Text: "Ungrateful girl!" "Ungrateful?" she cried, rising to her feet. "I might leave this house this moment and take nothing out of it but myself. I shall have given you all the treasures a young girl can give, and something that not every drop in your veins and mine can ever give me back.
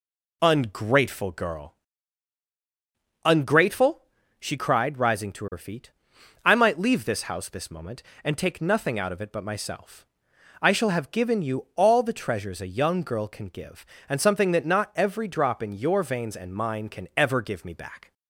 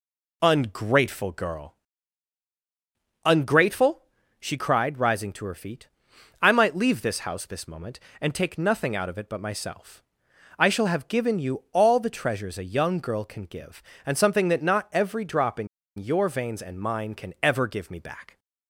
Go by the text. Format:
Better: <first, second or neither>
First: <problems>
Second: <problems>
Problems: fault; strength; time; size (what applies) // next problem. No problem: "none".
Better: first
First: none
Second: pauses between "in" and "your"; slight; at 15.6 s; 0.31 s long